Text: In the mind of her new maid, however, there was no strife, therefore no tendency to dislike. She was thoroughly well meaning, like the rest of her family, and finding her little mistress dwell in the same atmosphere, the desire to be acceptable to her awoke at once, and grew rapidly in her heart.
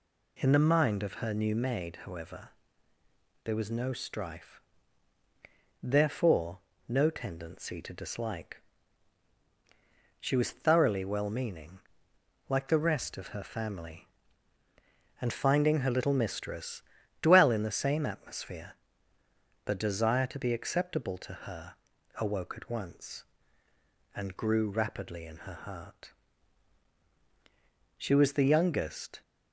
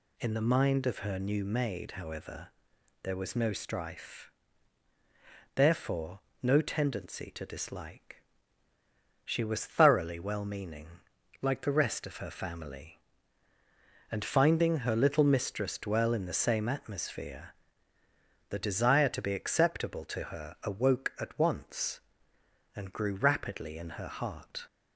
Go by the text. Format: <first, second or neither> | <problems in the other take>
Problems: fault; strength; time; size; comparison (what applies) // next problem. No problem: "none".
second | pauses between "therefore" and "no"; slight; at 6.5 s; 0.28 s long; slight in the second // pauses between "mistress" and "dwell"; slight; at 16.8 s; 0.36 s long // pauses between "her" and "awoke"; at 21.7 s; 0.44 s long // goes on to say "She was the youngest"; noticeable; from 27.9 s on; 1.2 s long